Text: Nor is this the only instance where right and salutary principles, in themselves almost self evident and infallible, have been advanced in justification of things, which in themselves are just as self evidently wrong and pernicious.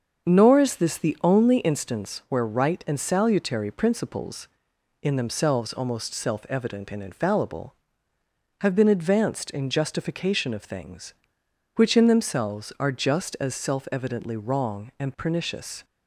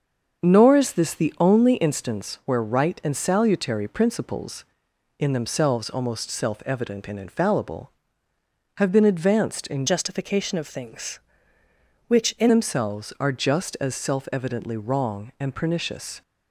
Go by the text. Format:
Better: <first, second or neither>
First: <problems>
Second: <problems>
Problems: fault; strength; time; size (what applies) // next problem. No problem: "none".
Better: first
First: starts louder than the rest; until 1.3 s; 6.5 dB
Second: starts louder than the rest; until 1.4 s; 6.5 dB // changes voice from "justification" to "in"; from 9.8 to 12.5 s; 2.7 s long